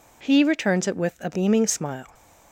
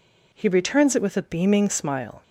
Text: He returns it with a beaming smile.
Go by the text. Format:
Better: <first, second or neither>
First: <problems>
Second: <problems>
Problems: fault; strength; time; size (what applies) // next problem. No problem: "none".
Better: neither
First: none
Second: none